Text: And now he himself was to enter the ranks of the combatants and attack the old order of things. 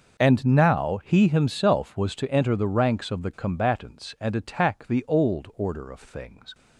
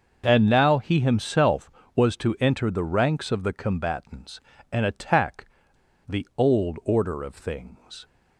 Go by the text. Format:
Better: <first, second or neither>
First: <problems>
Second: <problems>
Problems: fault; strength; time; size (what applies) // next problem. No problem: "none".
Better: first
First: starts louder than the rest; noticeable; until 1.2 s; 6 dB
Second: starts louder than the rest; until 1.2 s; 6.5 dB // pauses between "attack" and "the"; noticeable; at 5.4 s; 0.62 s long